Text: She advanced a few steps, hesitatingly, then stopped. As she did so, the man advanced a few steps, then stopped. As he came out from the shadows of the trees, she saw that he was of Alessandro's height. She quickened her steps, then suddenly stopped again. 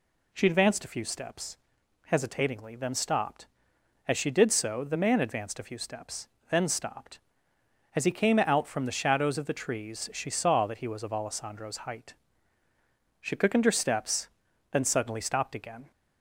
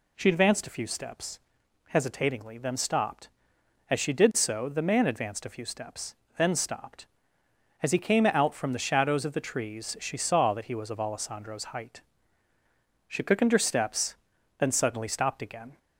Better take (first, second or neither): neither